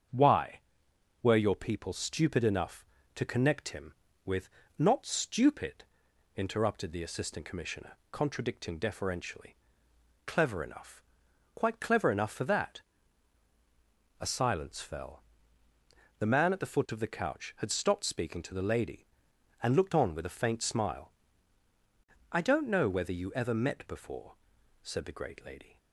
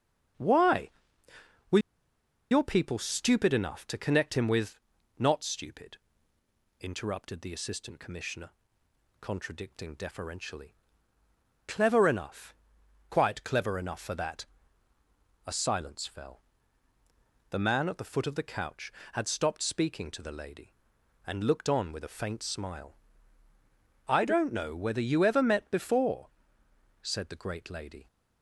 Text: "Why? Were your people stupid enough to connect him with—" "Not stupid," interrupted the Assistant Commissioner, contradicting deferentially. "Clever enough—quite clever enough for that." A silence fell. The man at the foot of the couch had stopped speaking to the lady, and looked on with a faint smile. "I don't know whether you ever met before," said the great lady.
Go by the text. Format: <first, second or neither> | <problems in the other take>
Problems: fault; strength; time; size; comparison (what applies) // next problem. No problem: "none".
first | starts louder than the rest; until 2.9 s; 7 dB; strong in the first // pauses between "Were" and "your"; noticeable; at 1.7 s; 0.72 s long